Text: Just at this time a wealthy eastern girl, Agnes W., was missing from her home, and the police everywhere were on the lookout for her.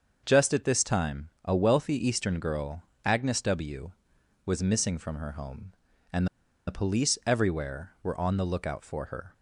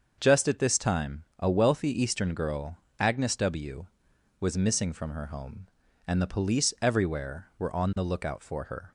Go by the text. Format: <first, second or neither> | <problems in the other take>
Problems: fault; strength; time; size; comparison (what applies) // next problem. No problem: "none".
second | starts louder than the rest; until 1.2 s; 6.5 dB; also in the second // pauses between "time" and "a"; slight; at 1.2 s; 0.16 s long; slight in the second // pauses between "and" and "the"; at 6.2 s; 0.41 s long